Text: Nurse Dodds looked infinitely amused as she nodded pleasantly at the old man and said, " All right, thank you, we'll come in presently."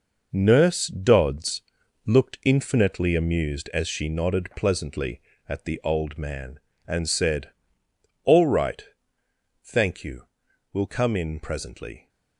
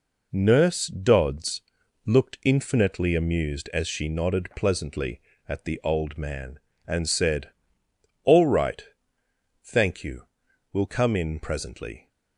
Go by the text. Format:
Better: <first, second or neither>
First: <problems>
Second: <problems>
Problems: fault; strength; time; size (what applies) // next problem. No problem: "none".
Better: second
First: gets quieter; strong; throughout; 12 dB // pauses between "Dodds" and "looked"; at 1.6 s; 0.44 s long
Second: pauses between "Dodds" and "looked"; at 1.6 s; 0.44 s long